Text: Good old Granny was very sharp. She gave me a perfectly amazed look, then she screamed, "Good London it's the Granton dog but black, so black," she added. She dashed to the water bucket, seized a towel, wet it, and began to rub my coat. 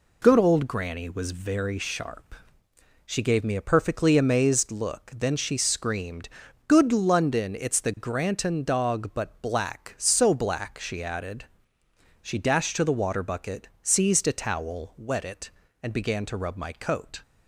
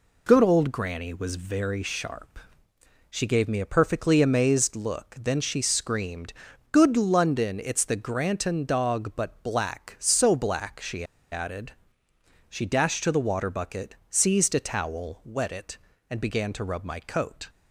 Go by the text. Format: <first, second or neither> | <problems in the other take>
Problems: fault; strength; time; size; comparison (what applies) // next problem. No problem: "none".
first | pauses between "she" and "added"; slight; at 11.0 s; 0.26 s long